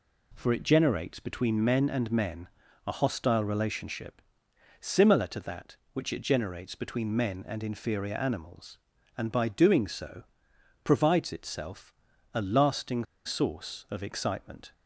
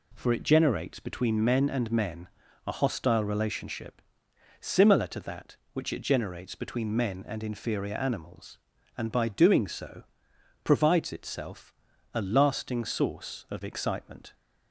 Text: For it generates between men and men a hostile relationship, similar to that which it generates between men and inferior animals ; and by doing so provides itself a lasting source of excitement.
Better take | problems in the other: second | pauses between "men" and "a"; at 2.4 s; 0.38 s long; also in the second // pauses between "so" and "provides"; noticeable; at 10.2 s; 0.62 s long; noticeable in the second // pauses between "itself" and "a"; at 11.9 s; 0.40 s long; also in the second // pauses between "lasting" and "source"; slight; at 13.0 s; 0.20 s long

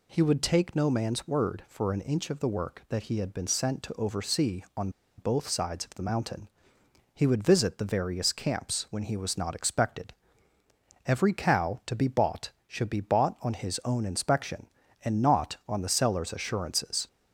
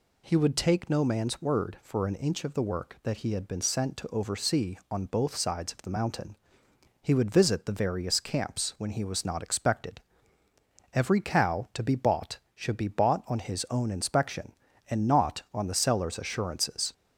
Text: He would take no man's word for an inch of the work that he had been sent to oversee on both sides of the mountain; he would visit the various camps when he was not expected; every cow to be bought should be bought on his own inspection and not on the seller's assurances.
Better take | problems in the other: second | pauses between "on" and "both"; slight; at 4.8 s; 0.28 s long

